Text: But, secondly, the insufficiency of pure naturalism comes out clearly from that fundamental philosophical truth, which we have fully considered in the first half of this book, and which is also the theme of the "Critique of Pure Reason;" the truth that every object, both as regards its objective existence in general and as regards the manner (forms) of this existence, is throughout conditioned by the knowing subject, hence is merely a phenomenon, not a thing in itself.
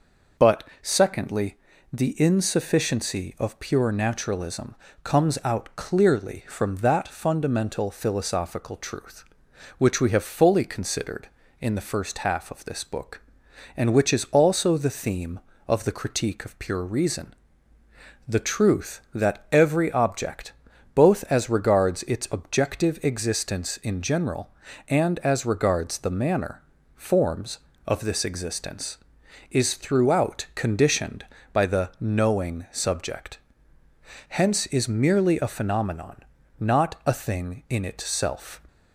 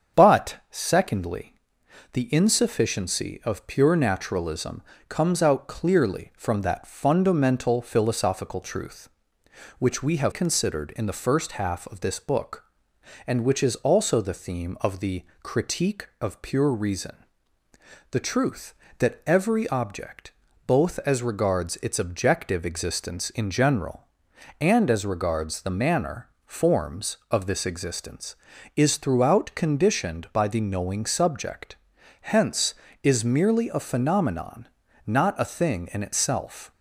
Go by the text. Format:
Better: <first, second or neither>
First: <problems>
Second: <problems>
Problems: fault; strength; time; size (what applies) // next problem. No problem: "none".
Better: first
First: pauses between "naturalism" and "comes"; slight; at 4.7 s; 0.28 s long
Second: starts louder than the rest; strong; until 1.2 s; 7.5 dB // pauses between "naturalism" and "comes"; slight; at 4.8 s; 0.28 s long // skips "fully"; at 10.3 s // pauses between "the" and "Critique"; slight; at 15.2 s; 0.18 s long